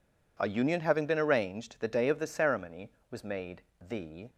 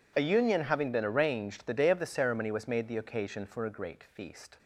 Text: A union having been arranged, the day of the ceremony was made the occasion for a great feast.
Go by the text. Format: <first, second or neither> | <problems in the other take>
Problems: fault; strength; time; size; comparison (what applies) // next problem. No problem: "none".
second | pauses between "made" and "the"; slight; at 3.6 s; 0.20 s long // stops before "occasion for a great feast"; at 4.2 s